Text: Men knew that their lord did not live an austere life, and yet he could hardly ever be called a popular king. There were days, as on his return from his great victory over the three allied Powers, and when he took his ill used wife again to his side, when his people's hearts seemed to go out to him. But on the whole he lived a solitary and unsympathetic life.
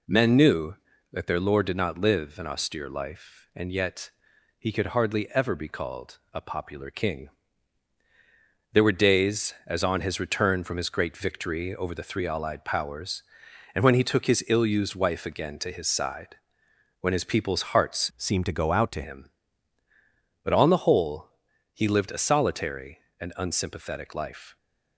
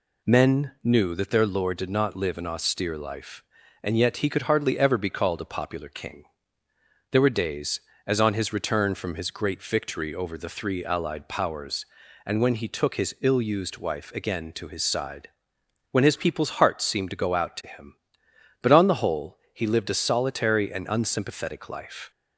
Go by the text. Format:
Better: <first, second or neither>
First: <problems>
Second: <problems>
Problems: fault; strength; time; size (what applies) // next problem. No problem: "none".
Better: second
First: pauses between "yet" and "he"; noticeable; at 4.1 s; 0.48 s long // changes voice from "seemed" to "to"; from 18.1 to 19.0 s; 0.9 s long // pauses between "whole" and "he"; noticeable; at 21.2 s; 0.46 s long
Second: pauses between "whole" and "he"; slight; at 19.3 s; 0.16 s long